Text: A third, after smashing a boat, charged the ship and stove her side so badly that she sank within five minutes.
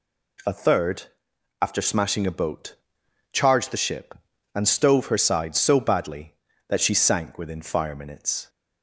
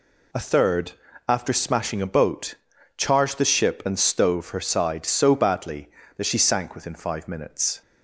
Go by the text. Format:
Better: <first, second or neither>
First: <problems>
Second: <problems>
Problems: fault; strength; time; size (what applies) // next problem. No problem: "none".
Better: second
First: says "fire" for "five"; at 7.6 s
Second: none